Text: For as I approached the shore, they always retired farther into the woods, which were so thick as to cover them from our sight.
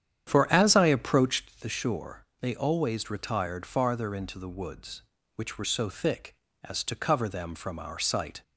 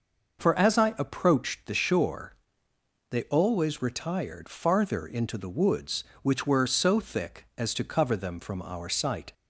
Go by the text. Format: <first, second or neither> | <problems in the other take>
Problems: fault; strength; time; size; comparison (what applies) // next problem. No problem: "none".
second | starts louder than the rest; strong; until 1.6 s; 9.5 dB